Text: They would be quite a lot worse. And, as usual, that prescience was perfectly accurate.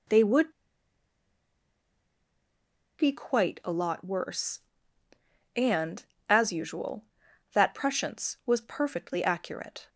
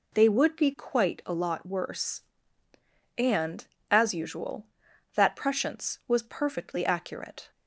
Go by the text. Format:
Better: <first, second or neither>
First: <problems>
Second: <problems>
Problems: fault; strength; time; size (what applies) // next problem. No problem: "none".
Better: second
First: pauses between "would" and "be"; strong; at 0.5 s; 2.4 s long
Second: none